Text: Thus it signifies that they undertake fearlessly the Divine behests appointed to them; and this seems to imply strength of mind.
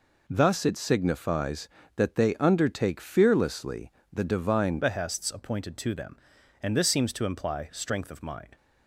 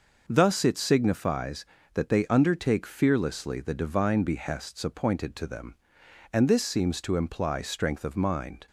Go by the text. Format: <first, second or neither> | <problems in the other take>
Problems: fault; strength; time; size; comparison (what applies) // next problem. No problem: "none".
second | pauses between "fearlessly" and "the"; slight; at 3.9 s; 0.20 s long // changes voice at "behests"; from 4.8 s on; 3.7 s long